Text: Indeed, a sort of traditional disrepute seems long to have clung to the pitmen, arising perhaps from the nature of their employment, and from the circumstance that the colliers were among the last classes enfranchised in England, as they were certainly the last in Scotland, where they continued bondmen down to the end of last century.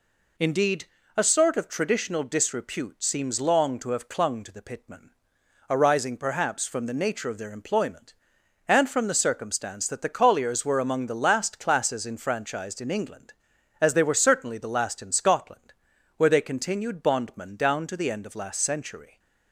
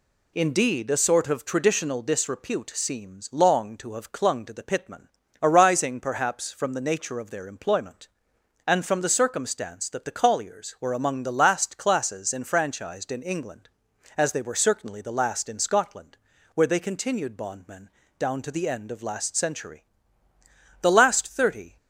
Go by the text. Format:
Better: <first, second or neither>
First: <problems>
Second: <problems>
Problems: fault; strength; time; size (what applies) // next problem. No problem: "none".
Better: first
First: none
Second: pauses between "bondmen" and "down"; slight; at 17.8 s; 0.30 s long // goes on to say "The last thirty"; noticeable; from 20.8 s on; 0.96 s long